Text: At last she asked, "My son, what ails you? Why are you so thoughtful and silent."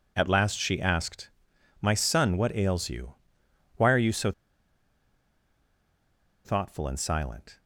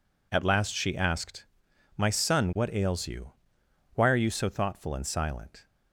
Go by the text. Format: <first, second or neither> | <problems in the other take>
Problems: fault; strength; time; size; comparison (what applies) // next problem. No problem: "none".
second | pauses between "so" and "thoughtful"; strong; at 4.3 s; 2.1 s long